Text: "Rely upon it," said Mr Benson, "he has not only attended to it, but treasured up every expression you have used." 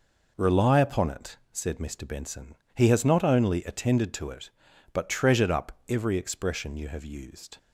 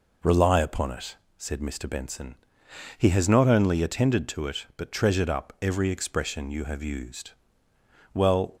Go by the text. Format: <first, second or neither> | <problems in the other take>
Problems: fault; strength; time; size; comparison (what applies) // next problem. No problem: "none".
first | goes on to say "Well"; slight; from 8.1 s on; 0.42 s long